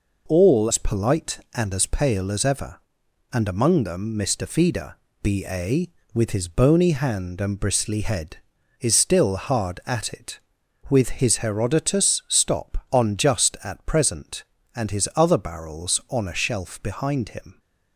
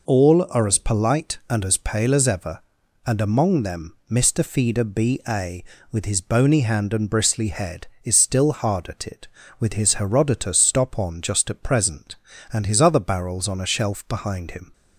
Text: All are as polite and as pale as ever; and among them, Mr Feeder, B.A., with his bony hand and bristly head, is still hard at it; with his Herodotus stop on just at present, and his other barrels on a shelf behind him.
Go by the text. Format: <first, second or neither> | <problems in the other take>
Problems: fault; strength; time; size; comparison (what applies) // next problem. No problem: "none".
second | skips "are"; at 0.6 s